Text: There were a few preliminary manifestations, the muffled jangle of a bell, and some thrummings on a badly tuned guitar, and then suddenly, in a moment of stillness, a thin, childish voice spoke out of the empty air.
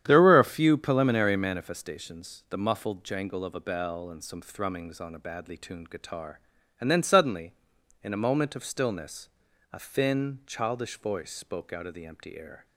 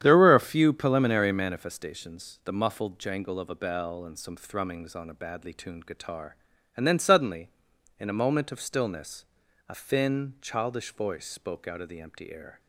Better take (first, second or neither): neither